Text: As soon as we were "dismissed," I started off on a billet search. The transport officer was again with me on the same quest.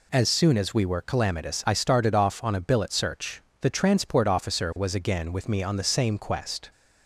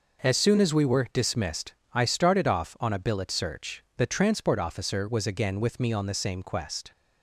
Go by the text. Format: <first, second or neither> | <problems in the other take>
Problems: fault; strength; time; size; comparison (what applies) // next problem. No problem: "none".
second | says "calamitous" for "dismissed"; at 1.0 s